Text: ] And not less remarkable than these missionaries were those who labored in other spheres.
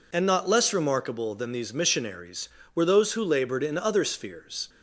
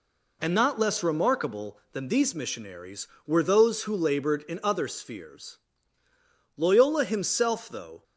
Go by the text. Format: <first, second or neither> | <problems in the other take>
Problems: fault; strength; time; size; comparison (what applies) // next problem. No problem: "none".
first | goes on to say "Loyola himself though"; from 6.5 s on; 1.4 s long